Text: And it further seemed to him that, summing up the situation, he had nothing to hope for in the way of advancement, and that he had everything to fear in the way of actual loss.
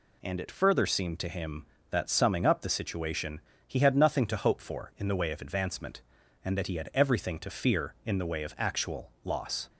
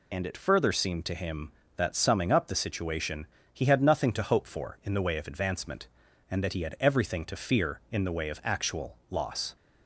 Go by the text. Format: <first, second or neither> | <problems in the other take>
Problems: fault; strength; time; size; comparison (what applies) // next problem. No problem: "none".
first | loses the start of "And"; at 0.1 s; 45 ms